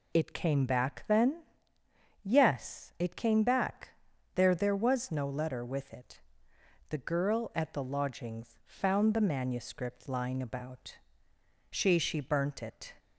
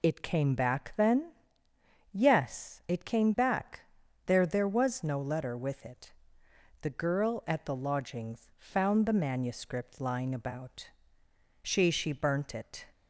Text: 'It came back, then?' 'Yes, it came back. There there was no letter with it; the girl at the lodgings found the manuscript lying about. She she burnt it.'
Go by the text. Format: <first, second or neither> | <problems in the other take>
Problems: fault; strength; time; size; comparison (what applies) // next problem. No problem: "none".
neither | none